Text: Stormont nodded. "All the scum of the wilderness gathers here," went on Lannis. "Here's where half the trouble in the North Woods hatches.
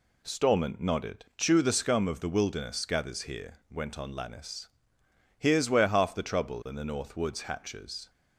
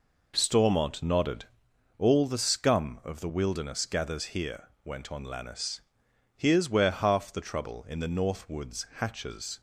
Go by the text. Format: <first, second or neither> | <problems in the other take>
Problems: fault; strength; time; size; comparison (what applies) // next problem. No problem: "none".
second | says "Chew" for "All"; at 1.3 s